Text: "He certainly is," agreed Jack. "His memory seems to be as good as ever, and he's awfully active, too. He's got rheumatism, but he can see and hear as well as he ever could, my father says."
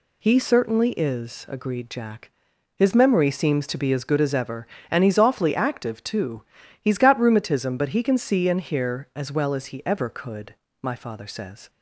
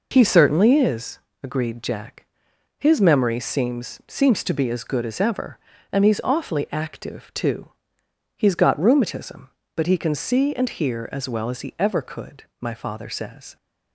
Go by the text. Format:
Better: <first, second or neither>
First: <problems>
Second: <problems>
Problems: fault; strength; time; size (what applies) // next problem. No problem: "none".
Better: first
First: none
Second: says "seems" twice; at 4.0 s